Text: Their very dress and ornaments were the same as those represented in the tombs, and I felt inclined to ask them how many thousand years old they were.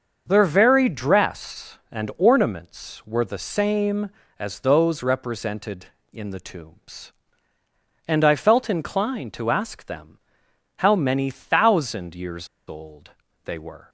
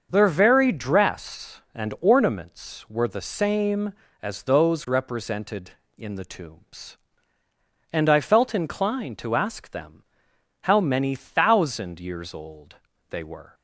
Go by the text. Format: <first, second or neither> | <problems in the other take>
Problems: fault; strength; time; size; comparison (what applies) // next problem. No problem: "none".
second | starts louder than the rest; until 1.2 s; 6.5 dB; also in the second // pauses between "them" and "how"; noticeable; at 10.1 s; 0.60 s long; noticeable in the second // pauses between "years" and "old"; slight; at 12.4 s; 0.21 s long // pauses between "old" and "they"; slight; at 13.1 s; 0.32 s long; slight in the second